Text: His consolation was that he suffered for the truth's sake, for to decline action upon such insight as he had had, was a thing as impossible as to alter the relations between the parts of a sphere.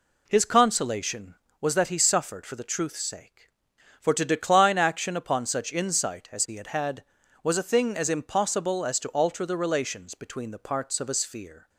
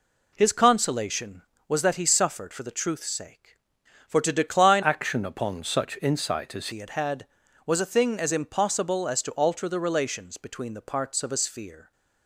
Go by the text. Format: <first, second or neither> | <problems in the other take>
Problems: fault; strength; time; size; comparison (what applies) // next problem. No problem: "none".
first | changes voice from "action" to "as"; from 4.8 to 6.6 s; 1.8 s long